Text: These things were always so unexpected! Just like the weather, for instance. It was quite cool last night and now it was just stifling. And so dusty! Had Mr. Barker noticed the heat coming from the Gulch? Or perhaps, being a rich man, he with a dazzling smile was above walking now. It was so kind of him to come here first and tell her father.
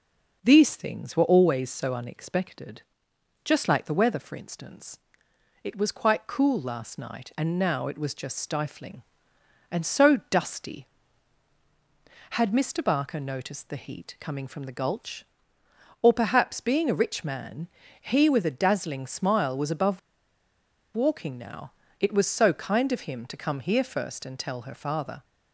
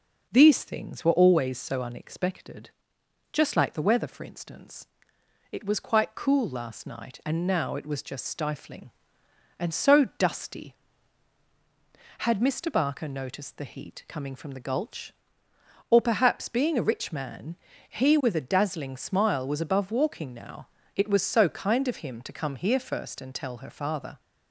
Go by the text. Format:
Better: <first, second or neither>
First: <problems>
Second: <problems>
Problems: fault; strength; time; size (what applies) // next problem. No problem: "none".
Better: second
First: pauses between "above" and "walking"; noticeable; at 19.9 s; 0.94 s long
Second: none